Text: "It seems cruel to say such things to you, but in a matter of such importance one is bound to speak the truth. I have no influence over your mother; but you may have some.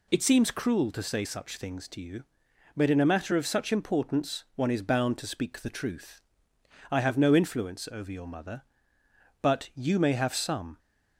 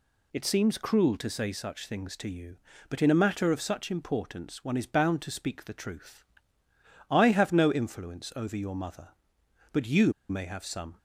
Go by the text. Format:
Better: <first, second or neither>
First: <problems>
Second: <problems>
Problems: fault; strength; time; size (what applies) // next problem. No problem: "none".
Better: first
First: none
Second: pauses between "you" and "may"; slight; at 10.1 s; 0.17 s long